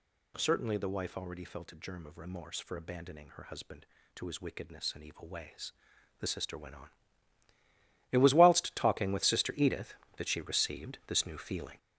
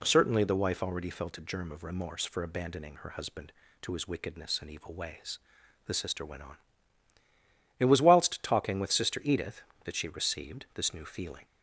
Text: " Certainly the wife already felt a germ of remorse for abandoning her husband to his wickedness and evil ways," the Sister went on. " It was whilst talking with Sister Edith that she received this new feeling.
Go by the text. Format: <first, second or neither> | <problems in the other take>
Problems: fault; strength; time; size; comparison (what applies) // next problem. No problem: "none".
second | gets louder; noticeable; throughout; 5 dB